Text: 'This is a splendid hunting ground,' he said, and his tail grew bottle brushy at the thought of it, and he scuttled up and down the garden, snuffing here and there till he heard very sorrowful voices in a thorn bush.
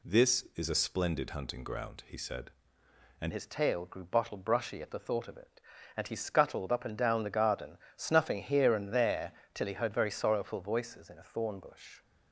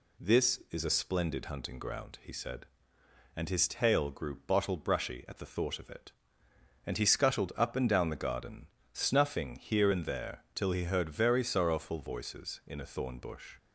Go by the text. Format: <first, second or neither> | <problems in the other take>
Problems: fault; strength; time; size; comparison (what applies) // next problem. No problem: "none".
second | changes voice at "his"; from 3.3 s on; 8.7 s long // pauses between "there" and "till"; slight; at 9.3 s; 0.24 s long